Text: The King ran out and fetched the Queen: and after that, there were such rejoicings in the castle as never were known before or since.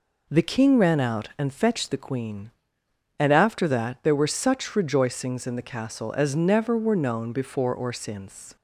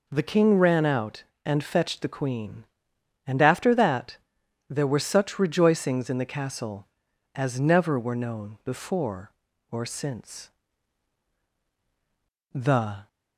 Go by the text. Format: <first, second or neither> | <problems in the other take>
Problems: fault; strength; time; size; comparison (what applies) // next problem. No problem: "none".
first | goes on to say "The"; from 12.5 s on; 0.54 s long